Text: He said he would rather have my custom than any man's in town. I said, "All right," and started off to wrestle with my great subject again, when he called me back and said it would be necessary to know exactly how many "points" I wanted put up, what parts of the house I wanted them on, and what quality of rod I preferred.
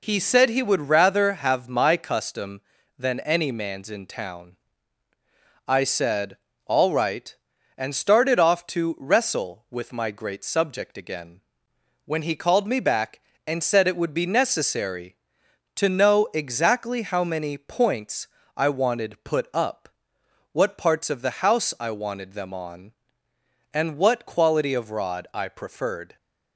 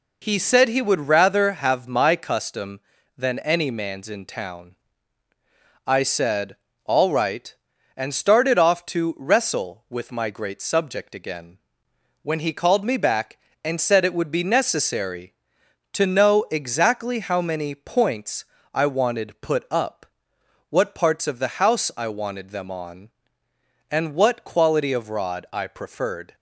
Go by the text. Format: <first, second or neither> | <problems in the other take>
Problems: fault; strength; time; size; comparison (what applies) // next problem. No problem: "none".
neither | pauses between "points" and "I"; slight; the same in both